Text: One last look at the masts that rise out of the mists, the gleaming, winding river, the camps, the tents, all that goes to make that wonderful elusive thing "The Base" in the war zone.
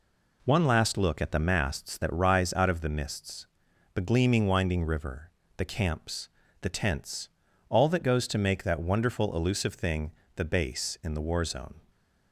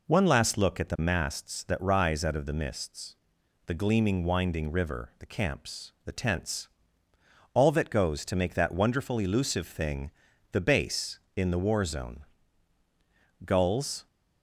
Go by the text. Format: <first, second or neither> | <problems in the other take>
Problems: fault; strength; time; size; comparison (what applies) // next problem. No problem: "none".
first | pauses between "thing" and "The"; at 10.0 s; 0.42 s long; slight in the first // goes on to say "Gulls"; noticeable; from 13.4 s on; 0.62 s long